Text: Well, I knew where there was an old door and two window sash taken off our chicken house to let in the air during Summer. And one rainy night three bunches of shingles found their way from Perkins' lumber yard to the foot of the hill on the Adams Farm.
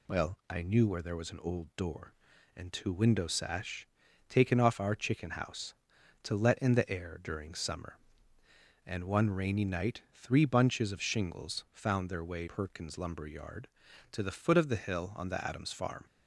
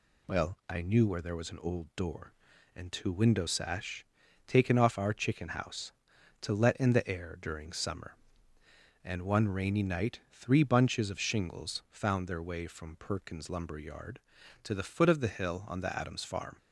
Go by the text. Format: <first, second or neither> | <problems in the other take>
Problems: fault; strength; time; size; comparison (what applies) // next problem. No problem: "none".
second | pauses between "sash" and "taken"; at 3.8 s; 0.42 s long; also in the second // skips "from"; at 12.4 s